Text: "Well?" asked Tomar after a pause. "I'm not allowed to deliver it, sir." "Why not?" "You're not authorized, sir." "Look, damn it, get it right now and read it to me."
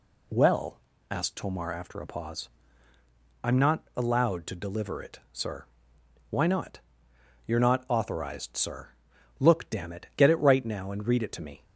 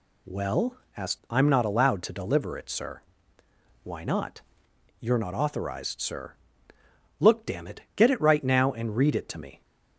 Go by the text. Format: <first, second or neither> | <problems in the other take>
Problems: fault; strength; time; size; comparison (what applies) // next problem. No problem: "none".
first | skips "Tomar after a pause"; at 1.2 s